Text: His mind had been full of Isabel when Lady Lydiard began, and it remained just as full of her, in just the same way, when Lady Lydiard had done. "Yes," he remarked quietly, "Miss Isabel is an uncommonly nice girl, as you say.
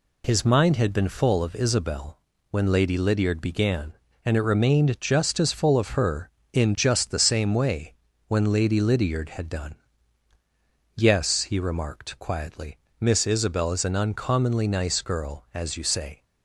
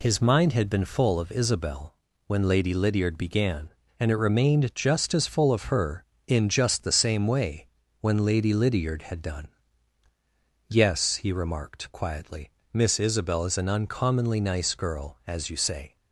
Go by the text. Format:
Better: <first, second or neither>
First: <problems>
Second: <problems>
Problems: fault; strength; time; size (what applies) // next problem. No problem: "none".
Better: neither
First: pauses between "Isabel" and "when"; slight; at 2.1 s; 0.32 s long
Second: pauses between "Isabel" and "when"; slight; at 1.9 s; 0.32 s long